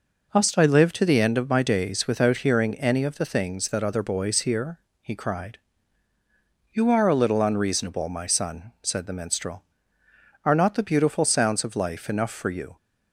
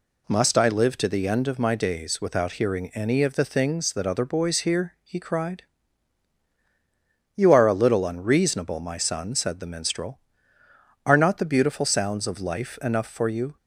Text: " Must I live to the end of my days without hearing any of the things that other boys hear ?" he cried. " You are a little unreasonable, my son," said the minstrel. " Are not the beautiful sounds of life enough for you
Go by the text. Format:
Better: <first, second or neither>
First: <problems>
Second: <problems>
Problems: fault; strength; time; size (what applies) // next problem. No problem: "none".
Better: neither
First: none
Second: none